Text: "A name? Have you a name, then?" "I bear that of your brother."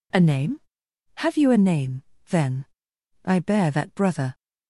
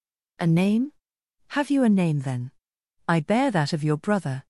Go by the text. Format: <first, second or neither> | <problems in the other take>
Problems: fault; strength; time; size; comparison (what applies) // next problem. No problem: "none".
second | skips "of your"; at 3.9 s